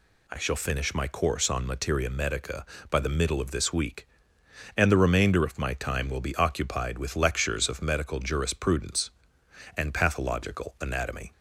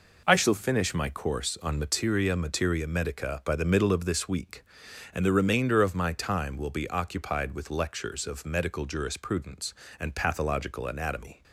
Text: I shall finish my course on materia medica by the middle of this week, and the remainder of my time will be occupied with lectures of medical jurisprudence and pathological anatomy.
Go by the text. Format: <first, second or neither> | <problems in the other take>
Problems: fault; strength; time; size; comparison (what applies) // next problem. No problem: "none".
first | says "materia" twice; at 2.3 s